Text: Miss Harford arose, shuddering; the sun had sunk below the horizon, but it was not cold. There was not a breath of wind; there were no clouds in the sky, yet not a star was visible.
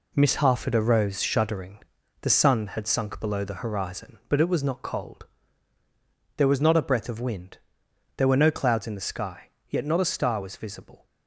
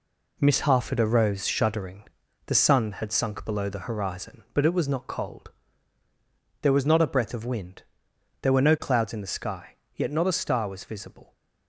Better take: neither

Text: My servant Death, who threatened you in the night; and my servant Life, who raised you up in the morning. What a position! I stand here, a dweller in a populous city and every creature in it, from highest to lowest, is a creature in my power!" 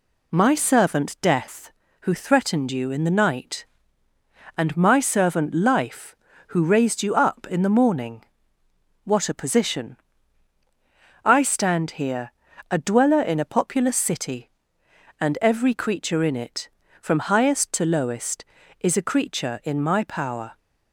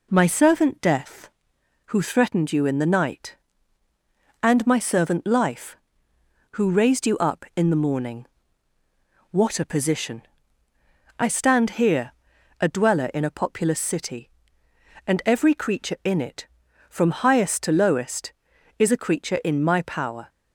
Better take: neither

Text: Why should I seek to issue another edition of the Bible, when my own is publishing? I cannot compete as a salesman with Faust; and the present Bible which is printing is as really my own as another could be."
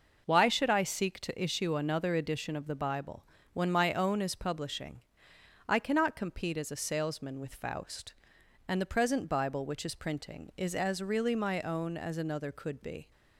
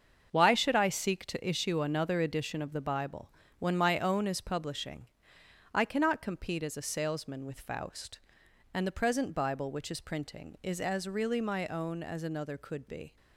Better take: first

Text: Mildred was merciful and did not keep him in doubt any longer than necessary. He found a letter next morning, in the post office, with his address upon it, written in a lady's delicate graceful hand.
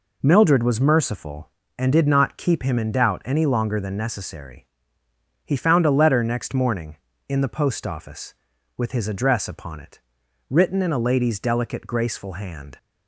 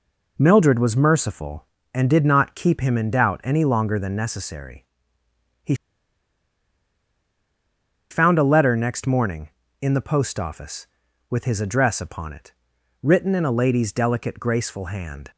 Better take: first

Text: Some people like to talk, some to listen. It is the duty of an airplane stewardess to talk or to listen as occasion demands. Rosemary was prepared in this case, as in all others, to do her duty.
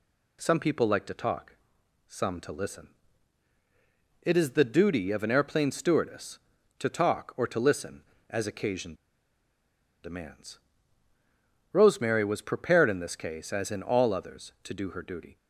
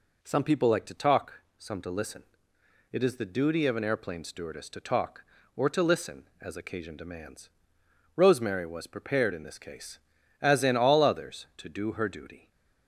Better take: second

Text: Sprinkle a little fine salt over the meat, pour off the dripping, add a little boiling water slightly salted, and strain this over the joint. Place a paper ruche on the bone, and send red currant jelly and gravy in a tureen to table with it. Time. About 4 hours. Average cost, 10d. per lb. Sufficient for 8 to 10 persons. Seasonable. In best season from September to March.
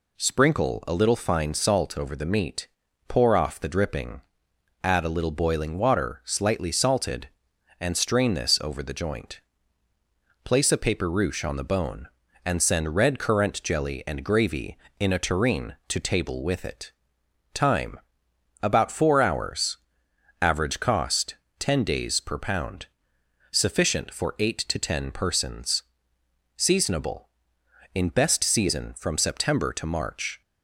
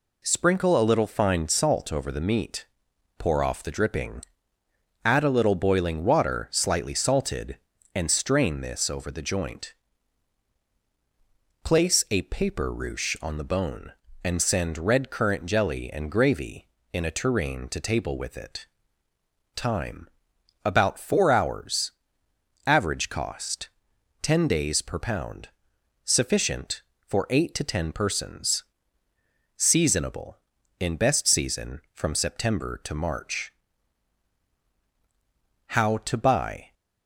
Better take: first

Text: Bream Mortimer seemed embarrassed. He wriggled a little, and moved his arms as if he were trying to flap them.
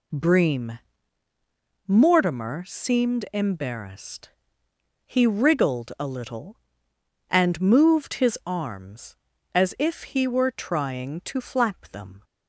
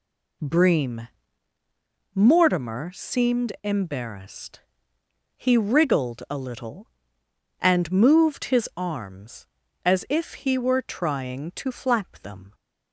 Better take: neither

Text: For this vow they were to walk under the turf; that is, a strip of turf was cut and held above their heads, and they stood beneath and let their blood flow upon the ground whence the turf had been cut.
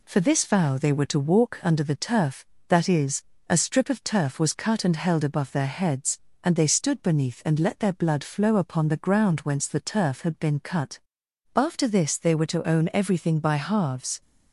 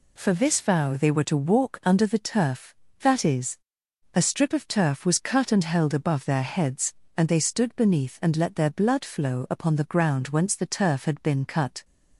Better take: second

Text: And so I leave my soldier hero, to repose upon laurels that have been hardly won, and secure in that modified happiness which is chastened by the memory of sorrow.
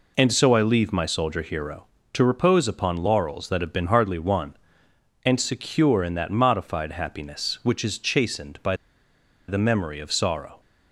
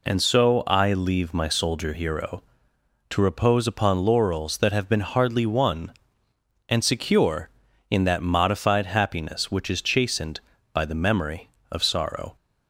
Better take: second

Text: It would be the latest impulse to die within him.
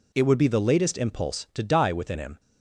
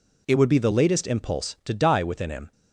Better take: neither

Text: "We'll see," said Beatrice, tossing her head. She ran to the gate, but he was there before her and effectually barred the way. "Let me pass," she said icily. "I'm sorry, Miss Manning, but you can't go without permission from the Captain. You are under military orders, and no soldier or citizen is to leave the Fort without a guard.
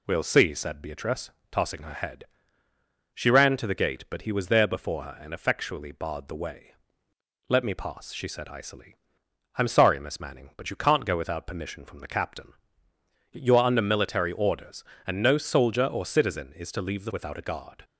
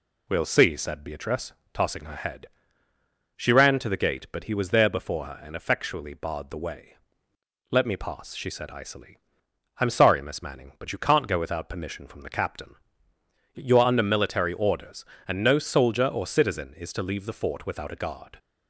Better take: second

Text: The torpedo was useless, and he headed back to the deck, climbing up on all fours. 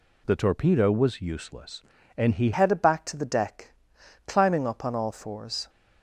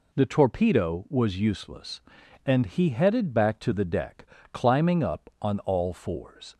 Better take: second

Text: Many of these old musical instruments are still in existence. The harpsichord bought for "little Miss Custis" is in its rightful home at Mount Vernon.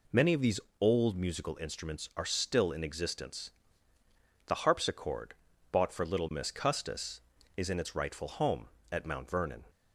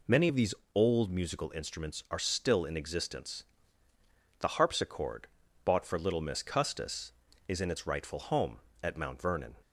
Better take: neither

